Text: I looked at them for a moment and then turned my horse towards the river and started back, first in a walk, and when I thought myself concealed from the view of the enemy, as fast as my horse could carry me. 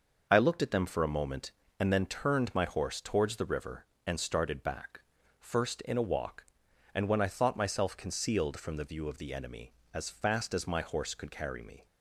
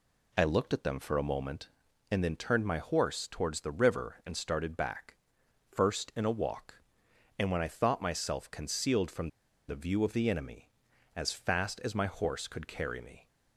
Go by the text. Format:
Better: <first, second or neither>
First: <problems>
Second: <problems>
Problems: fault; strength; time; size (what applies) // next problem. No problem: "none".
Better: first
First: none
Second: pauses between "from" and "the"; at 9.2 s; 0.40 s long